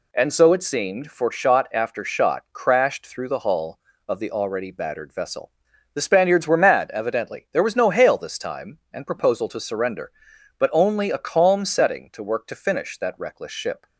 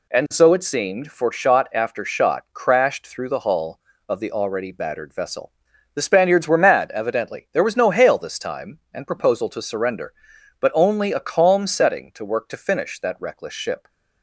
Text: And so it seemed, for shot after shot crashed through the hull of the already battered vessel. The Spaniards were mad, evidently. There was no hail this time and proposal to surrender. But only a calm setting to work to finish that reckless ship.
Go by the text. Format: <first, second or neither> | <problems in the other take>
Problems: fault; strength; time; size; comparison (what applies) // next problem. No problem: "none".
neither | none